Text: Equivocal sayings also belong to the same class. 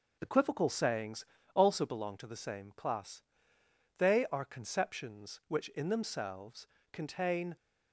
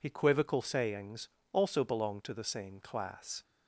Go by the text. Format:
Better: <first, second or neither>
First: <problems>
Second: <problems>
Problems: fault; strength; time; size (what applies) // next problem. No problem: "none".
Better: second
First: pauses between "sayings" and "also"; slight; at 1.2 s; 0.28 s long // goes on to say "They are conceptions which in themselves contain"; strong; from 3.9 s on; 3.5 s long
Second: pauses between "sayings" and "also"; slight; at 1.2 s; 0.24 s long